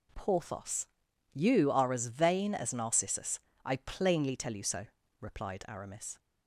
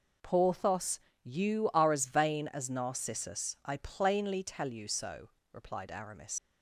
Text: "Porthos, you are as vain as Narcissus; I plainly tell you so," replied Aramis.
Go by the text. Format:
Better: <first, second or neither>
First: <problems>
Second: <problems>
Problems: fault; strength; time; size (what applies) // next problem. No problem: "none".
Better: first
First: none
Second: leaves "Aramis" unfinished; at 6.3 s; 95 ms